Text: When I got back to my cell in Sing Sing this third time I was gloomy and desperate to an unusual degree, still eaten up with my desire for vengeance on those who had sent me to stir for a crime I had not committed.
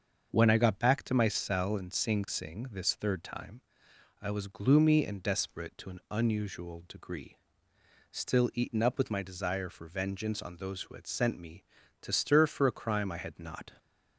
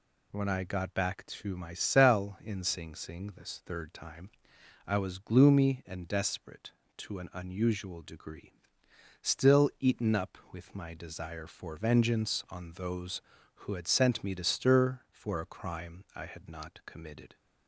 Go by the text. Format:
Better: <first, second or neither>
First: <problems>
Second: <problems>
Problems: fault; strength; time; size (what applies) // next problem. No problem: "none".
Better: second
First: starts louder than the rest; until 1.3 s; 6.5 dB // pauses between "time" and "I"; noticeable; at 3.5 s; 0.60 s long // stops before "committed"; at 13.7 s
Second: pauses between "time" and "I"; noticeable; at 4.2 s; 0.56 s long